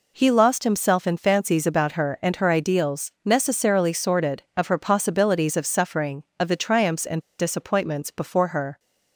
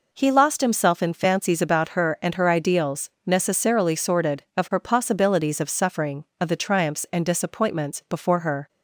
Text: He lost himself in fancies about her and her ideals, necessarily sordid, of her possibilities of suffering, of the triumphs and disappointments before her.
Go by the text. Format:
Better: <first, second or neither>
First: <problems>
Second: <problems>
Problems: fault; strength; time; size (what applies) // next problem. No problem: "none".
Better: second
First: pauses between "and" and "disappointments"; slight; at 7.1 s; 0.19 s long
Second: none